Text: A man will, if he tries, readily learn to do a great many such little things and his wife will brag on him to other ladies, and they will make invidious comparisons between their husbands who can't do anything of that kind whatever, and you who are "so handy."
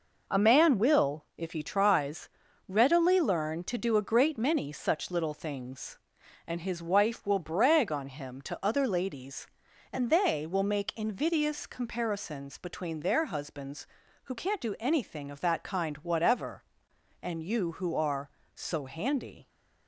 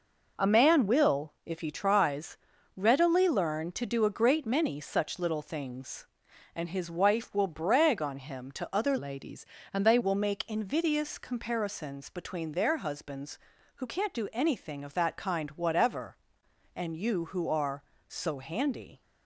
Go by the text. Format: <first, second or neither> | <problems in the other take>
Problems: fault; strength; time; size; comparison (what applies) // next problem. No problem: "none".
first | changes voice from "ladies" to "they"; from 8.9 to 9.9 s; 1.0 s long